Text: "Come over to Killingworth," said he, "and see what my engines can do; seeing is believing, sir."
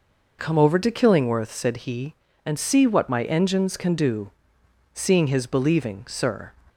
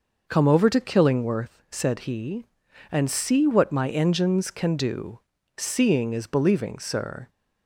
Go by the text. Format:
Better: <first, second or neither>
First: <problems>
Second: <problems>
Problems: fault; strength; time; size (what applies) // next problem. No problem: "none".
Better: second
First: says "his" for "is"; at 5.2 s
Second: none